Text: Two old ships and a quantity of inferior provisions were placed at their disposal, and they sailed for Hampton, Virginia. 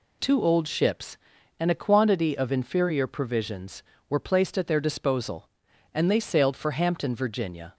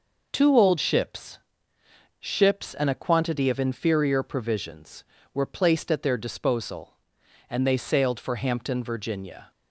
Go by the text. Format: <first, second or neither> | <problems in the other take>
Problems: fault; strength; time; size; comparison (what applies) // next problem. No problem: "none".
first | says "ships" twice; at 2.1 s